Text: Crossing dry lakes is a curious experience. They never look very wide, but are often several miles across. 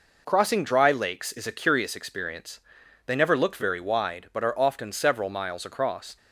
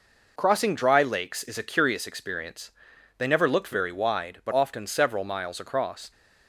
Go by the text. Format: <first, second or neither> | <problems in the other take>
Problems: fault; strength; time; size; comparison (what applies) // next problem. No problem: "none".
first | skips "are"; at 4.5 s